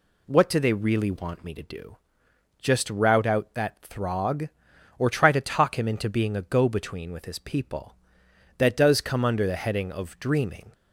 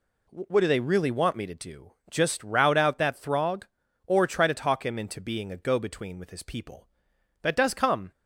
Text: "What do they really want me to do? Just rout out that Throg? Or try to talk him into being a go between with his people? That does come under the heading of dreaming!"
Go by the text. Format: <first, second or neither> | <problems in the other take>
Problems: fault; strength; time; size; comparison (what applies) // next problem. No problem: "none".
first | stops before "under the heading of dreaming"; at 8.1 s